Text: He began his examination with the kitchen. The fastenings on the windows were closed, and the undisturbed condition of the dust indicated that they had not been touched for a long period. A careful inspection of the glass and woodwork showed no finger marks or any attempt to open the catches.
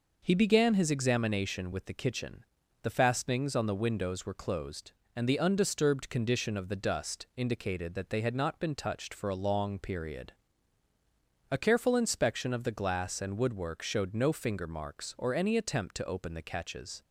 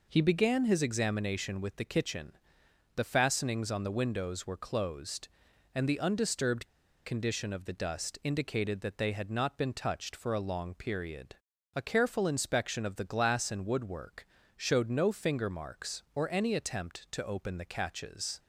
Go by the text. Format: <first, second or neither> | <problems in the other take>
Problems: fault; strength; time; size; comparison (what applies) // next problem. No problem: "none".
first | pauses between "undisturbed" and "condition"; at 6.6 s; 0.37 s long // pauses between "woodwork" and "showed"; slight; at 14.2 s; 0.30 s long